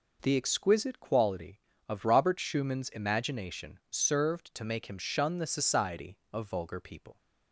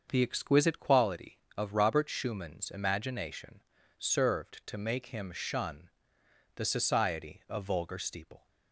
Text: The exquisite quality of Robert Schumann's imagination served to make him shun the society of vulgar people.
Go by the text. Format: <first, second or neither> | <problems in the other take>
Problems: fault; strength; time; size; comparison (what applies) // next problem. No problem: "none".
first | starts louder than the rest; until 1.1 s; 6.5 dB // pauses between "imagination" and "served"; at 3.5 s; 0.38 s long // pauses between "shun" and "the"; noticeable; at 5.8 s; 0.66 s long // says "steeple" for "people"; at 7.9 s